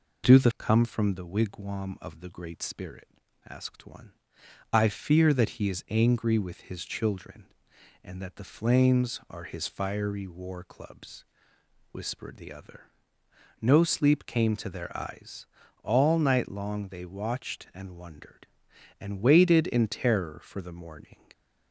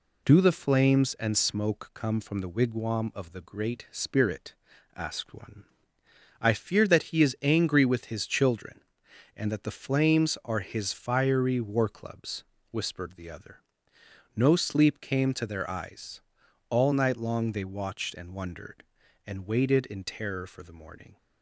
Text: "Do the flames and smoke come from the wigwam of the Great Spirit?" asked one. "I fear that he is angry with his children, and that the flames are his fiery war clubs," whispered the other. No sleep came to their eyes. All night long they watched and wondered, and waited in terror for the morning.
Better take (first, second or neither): second